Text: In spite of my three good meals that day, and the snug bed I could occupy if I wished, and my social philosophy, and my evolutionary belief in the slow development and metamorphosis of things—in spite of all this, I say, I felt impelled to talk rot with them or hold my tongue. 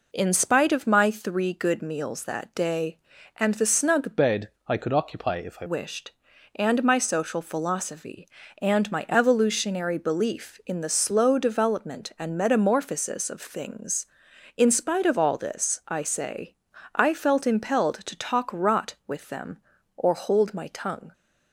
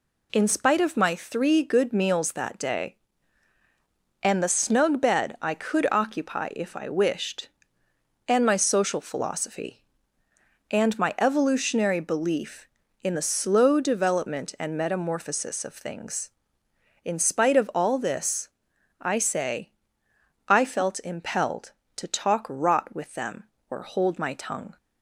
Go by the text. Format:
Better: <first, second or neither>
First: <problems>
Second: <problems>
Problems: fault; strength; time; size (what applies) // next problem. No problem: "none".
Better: second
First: changes voice from "bed" to "I"; from 4.1 to 5.6 s; 1.5 s long // pauses between "bed" and "I"; slight; at 4.4 s; 0.18 s long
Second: none